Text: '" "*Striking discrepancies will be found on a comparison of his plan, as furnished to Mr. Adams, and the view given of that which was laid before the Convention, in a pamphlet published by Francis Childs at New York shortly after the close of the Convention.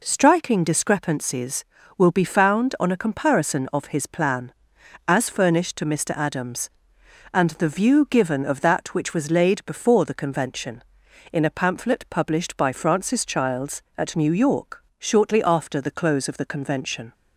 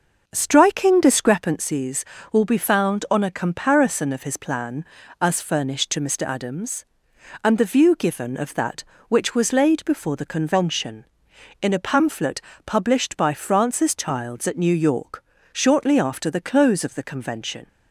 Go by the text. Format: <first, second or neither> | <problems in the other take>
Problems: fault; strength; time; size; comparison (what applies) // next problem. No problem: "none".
first | starts louder than the rest; noticeable; until 1.4 s; 5.5 dB // pauses between "pamphlet" and "published"; slight; at 12.4 s; 0.24 s long // pauses between "York" and "shortly"; slight; at 15.2 s; 0.30 s long; slight in the first